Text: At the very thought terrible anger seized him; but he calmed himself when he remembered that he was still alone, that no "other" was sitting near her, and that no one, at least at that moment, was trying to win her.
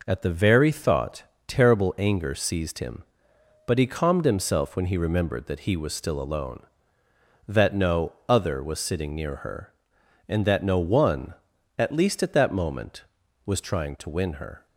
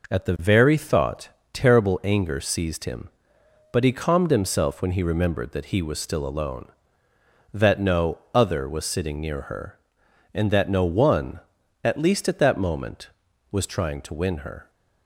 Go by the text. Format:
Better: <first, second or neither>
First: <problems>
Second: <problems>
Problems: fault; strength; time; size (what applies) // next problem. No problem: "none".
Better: neither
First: pauses between "thought" and "terrible"; slight; at 1.2 s; 0.22 s long // pauses between "no" and "other"; slight; at 8.1 s; 0.16 s long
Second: pauses between "thought" and "terrible"; slight; at 1.2 s; 0.22 s long // pauses between "no" and "other"; slight; at 8.1 s; 0.16 s long